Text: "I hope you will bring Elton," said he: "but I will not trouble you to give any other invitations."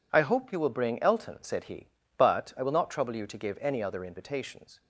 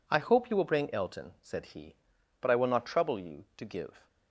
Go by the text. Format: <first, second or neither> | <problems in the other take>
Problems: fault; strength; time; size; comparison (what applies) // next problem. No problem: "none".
first | stops before "any other invitations"; at 4.0 s